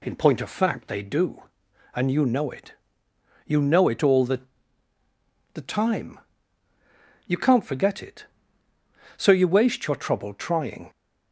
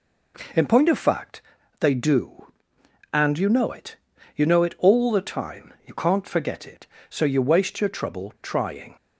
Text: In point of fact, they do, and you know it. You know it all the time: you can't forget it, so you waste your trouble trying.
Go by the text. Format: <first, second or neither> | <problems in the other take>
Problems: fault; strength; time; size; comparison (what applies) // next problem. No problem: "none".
second | says "the" twice; at 5.5 s